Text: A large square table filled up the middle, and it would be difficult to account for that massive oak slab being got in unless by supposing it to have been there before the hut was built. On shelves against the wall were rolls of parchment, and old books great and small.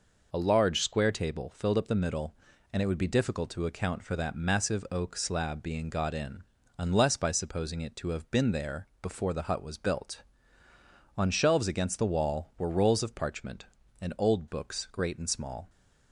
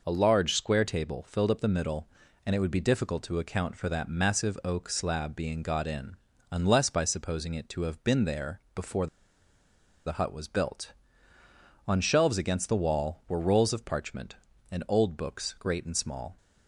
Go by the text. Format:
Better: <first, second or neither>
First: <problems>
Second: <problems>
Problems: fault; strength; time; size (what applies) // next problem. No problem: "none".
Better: first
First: pauses between "in" and "unless"; slight; at 6.4 s; 0.34 s long // pauses between "there" and "before"; slight; at 8.8 s; 0.16 s long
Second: pauses between "in" and "unless"; slight; at 6.1 s; 0.34 s long // pauses between "there" and "before"; slight; at 8.5 s; 0.16 s long // pauses between "before" and "the"; at 9.0 s; 0.98 s long